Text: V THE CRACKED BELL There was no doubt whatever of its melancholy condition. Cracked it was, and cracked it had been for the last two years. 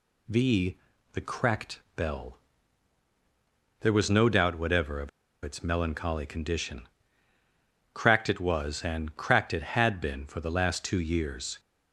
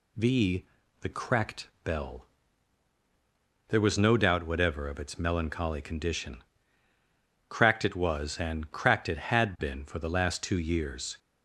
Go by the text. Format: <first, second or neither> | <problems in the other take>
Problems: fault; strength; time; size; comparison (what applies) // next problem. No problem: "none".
second | pauses between "V" and "THE"; slight; at 0.7 s; 0.36 s long; slight in the second // pauses between "CRACKED" and "BELL"; slight; at 1.7 s; 0.16 s long; slight in the second // pauses between "BELL" and "There"; strong; at 2.3 s; 1.4 s long; strong in the second // pauses between "of" and "its"; slight; at 5.0 s; 0.33 s long